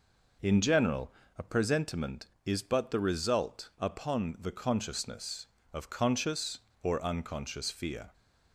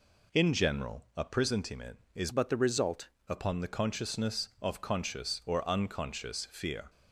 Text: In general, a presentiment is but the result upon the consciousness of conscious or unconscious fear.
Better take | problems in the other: first | changes voice from "but" to "result"; from 2.3 to 3.0 s; 0.7 s long

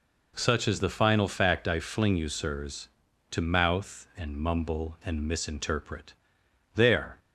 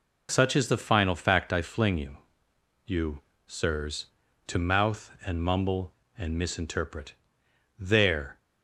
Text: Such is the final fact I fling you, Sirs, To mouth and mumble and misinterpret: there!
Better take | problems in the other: first | says "you" twice; at 2.8 s

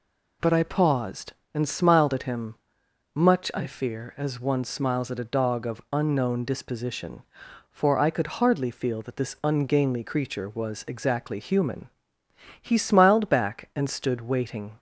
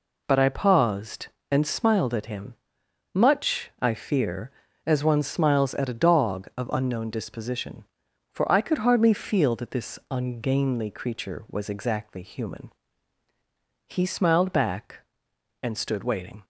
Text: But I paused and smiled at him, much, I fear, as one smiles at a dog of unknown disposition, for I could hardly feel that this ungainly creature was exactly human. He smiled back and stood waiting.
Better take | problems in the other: neither | none

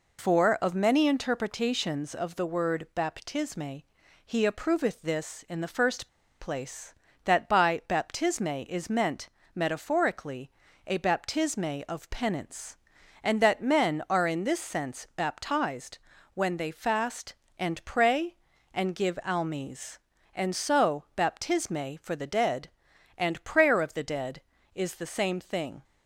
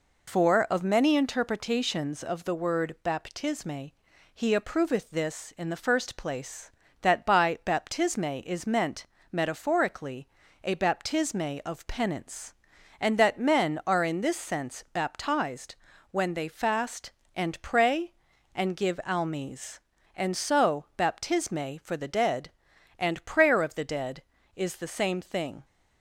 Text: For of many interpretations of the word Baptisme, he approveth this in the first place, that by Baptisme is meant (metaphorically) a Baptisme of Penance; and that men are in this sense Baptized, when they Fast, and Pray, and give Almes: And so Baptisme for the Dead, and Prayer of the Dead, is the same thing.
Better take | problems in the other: second | pauses between "first" and "place"; slight; at 6.0 s; 0.33 s long

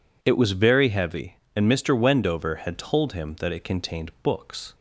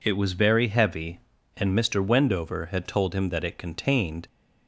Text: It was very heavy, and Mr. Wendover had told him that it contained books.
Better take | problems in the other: first | stops before "books"; at 4.2 s

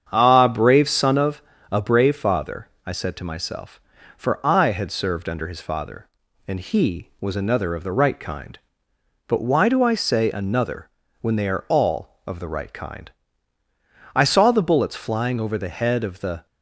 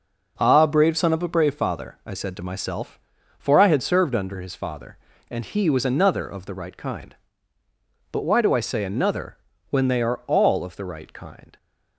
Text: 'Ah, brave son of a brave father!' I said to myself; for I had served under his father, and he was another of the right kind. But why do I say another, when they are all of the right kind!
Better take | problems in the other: second | starts louder than the rest; strong; until 1.1 s; 8 dB // pauses between "of" and "a"; slight; at 1.4 s; 0.30 s long // goes on to say "I saw the bullets flying over the head of the"; strong; from 14.1 s on; 2.3 s long

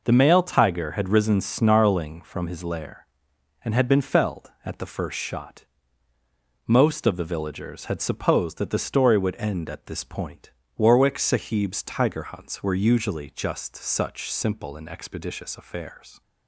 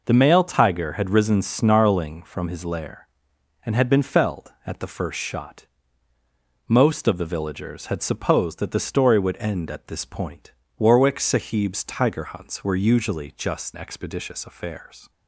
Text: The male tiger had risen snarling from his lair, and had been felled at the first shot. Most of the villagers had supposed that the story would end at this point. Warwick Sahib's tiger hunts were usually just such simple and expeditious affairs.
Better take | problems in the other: first | skips "such simple and"; at 13.7 s

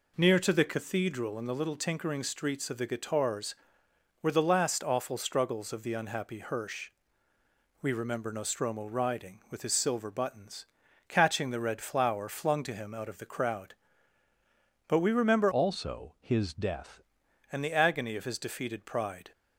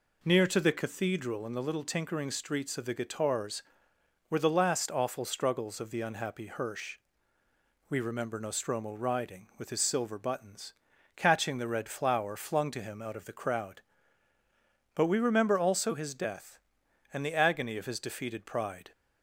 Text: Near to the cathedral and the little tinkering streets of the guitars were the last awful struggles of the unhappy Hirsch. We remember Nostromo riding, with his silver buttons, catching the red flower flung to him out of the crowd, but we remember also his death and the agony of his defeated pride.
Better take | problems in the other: second | changes voice from "also" to "death"; from 15.5 to 17.0 s; 1.5 s long

